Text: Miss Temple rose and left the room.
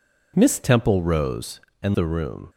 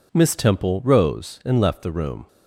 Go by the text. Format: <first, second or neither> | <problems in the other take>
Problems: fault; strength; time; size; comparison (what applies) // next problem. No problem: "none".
second | skips "left"; at 1.9 s